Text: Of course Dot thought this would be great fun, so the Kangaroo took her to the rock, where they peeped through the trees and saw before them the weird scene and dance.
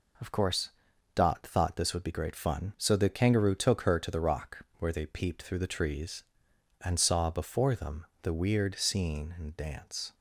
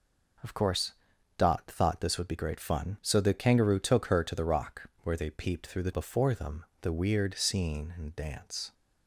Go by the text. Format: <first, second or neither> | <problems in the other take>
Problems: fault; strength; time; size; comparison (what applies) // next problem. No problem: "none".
first | pauses between "course" and "Dot"; at 0.9 s; 0.44 s long; also in the first // skips "trees and saw"; at 5.9 s // pauses between "them" and "the"; slight; at 6.6 s; 0.18 s long; slight in the first